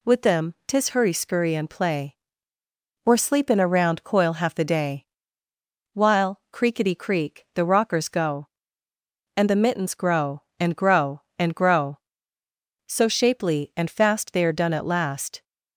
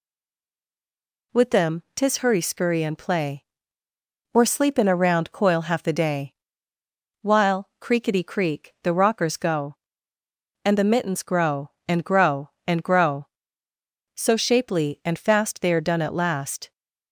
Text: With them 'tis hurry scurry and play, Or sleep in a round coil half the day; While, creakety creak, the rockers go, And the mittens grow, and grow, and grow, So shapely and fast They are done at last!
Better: first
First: none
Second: stays silent before the first word; noticeable; until 1.3 s; 1.3 s long

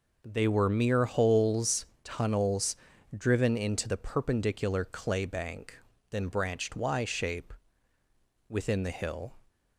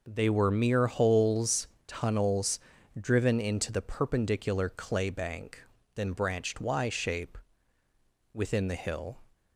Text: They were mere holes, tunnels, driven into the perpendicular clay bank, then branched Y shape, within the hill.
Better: neither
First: none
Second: none

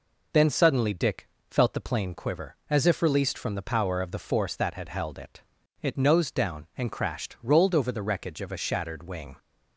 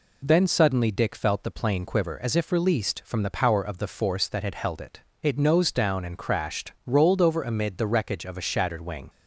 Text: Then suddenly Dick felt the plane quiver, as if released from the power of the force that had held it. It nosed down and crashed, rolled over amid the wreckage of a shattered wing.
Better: second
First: pauses between "Dick" and "felt"; slight; at 1.2 s; 0.22 s long // skips "amid"; at 7.9 s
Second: none

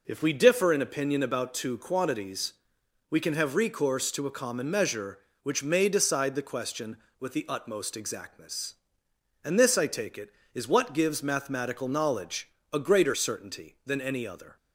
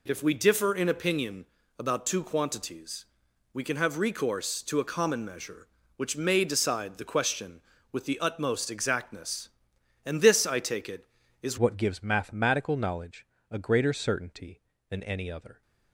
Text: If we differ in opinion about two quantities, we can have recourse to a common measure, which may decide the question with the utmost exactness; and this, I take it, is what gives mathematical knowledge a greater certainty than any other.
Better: first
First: pauses between "knowledge" and "a"; slight; at 12.4 s; 0.24 s long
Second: pauses between "opinion" and "about"; slight; at 1.4 s; 0.34 s long // changes voice at "what"; from 11.5 s on; 4.1 s long // pauses between "knowledge" and "a"; slight; at 13.2 s; 0.24 s long

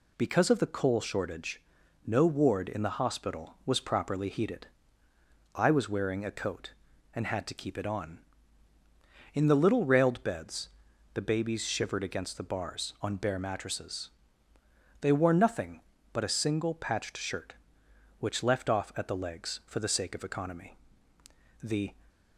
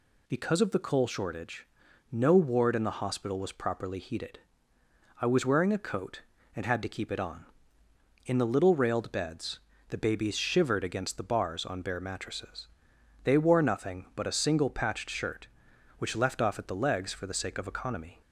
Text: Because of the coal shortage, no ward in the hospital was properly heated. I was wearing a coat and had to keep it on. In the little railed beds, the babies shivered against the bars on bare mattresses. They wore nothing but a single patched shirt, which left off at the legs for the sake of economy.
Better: second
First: goes on to say "The"; slight; from 21.6 s on; 0.34 s long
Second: none

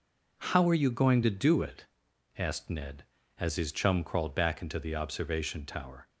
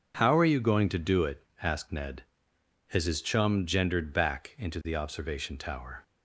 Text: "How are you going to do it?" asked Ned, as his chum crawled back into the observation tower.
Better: first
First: none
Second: says "gendered" for "crawled"; at 3.6 s

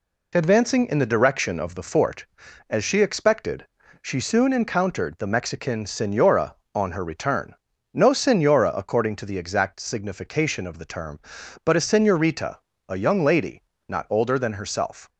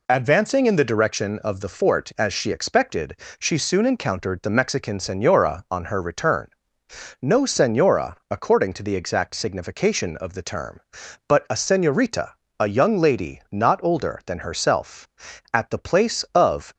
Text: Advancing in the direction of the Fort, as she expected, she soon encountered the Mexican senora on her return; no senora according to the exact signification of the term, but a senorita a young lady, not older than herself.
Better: first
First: pauses between "senorita" and "a"; slight; at 12.5 s; 0.28 s long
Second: pauses between "senorita" and "a"; slight; at 12.3 s; 0.26 s long // goes on to say "At the place of"; noticeable; from 15.5 s on; 1.2 s long

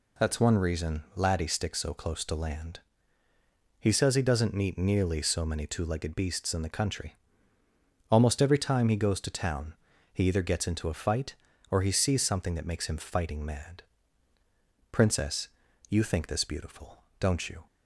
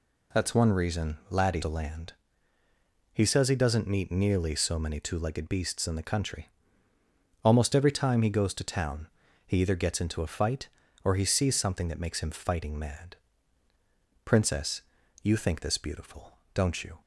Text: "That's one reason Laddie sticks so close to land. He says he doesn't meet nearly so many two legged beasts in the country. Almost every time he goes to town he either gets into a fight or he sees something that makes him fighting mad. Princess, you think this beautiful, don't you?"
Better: first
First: pauses between "town" and "he"; at 9.7 s; 0.38 s long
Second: skips "sticks so close"; at 1.6 s // pauses between "town" and "he"; at 9.0 s; 0.38 s long

